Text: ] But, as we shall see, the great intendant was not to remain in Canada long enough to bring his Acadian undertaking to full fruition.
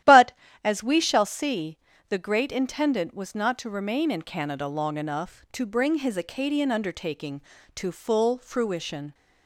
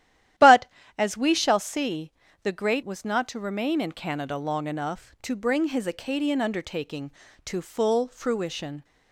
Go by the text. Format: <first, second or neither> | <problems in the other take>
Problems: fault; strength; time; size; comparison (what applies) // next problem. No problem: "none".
first | starts louder than the rest; strong; until 1.7 s; 12 dB; strong in the first // skips "intendant"; at 2.8 s